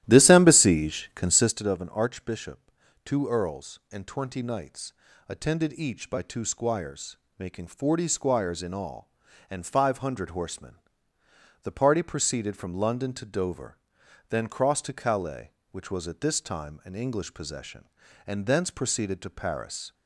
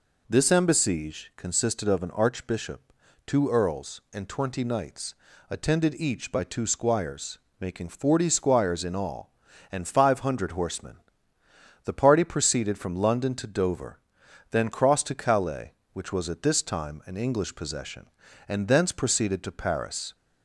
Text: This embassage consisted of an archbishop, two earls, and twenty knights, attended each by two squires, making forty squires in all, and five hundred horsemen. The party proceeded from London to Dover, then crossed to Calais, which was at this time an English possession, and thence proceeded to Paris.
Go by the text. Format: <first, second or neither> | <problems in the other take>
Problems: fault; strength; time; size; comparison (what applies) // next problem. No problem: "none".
second | starts louder than the rest; strong; until 1.7 s; 13 dB